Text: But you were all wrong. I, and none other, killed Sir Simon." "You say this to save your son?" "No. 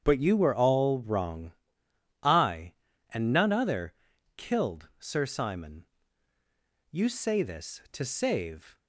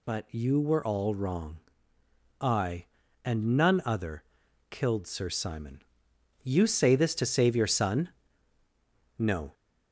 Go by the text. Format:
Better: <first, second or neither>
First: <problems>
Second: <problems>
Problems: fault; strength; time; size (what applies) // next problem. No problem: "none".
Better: second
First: starts louder than the rest; strong; until 1.0 s; 8 dB // stops before "your son No"; at 8.7 s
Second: none